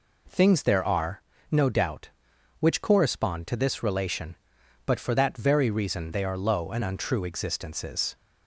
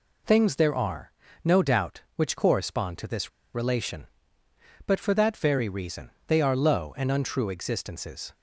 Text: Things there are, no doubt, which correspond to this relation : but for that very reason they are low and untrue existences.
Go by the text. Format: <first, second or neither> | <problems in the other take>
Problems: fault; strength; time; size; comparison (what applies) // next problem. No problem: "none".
first | pauses between "this" and "relation"; slight; at 3.2 s; 0.24 s long // pauses between "reason" and "they"; slight; at 6.0 s; 0.16 s long